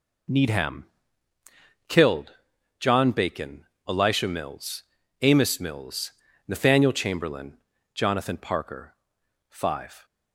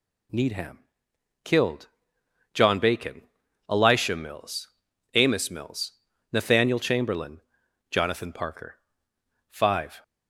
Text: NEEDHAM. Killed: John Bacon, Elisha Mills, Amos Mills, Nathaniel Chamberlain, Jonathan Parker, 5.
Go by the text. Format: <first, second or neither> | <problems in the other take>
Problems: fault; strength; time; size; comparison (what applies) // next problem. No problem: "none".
neither | none